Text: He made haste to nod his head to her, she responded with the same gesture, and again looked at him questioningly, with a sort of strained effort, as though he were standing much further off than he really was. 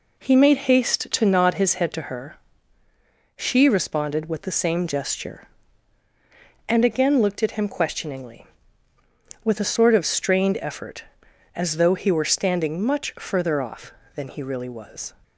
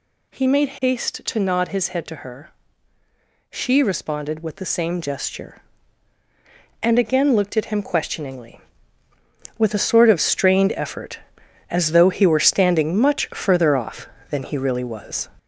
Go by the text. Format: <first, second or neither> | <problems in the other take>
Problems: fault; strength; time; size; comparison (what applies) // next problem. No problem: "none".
first | gets louder; noticeable; throughout; 5 dB